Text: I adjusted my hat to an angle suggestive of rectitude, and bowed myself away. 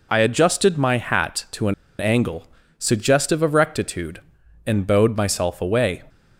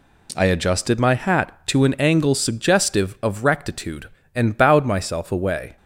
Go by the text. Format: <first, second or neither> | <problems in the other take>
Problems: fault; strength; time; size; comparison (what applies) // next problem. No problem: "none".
second | pauses between "an" and "angle"; slight; at 1.7 s; 0.26 s long // pauses between "angle" and "suggestive"; slight; at 2.4 s; 0.30 s long